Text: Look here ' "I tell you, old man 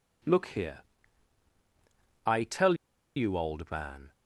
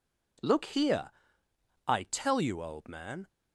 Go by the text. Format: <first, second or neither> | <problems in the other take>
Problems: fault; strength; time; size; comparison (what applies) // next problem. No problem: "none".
second | pauses between "tell" and "you"; at 2.7 s; 0.40 s long